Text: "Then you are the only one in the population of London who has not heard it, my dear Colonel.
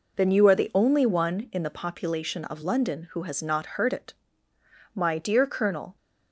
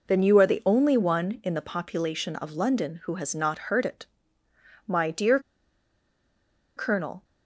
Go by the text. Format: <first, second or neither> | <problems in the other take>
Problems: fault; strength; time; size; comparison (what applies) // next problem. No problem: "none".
first | pauses between "dear" and "Colonel"; strong; at 5.3 s; 1.3 s long